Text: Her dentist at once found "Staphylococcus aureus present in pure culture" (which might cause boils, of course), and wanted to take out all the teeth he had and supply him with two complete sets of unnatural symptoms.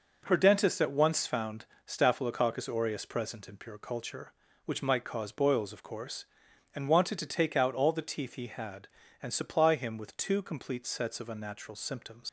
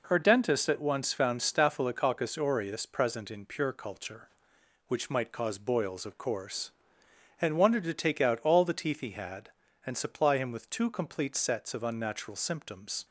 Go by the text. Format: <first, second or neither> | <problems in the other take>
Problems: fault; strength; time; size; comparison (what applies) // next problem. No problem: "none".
second | pauses between "found" and "Staphylococcus"; slight; at 1.6 s; 0.18 s long // leaves "symptoms" unfinished; at 12.2 s; 90 ms